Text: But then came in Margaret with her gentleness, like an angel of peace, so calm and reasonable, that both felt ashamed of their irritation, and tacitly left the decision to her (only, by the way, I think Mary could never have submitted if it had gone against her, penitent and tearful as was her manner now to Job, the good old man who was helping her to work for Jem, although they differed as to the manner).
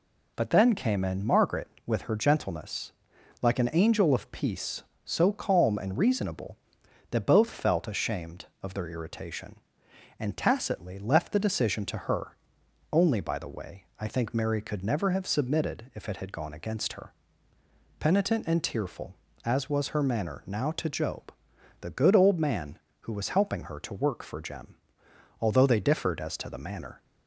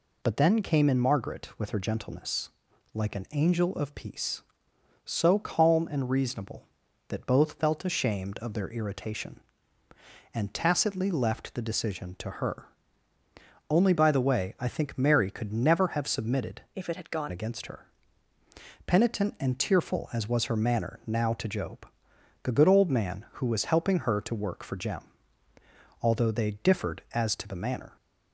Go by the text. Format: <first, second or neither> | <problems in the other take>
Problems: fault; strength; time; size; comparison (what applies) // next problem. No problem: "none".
first | changes voice from "if" to "gone"; from 16.7 to 17.3 s; 0.6 s long